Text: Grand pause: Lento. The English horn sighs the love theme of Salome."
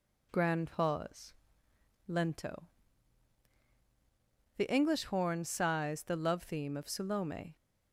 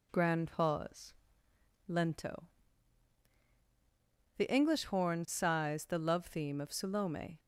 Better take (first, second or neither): neither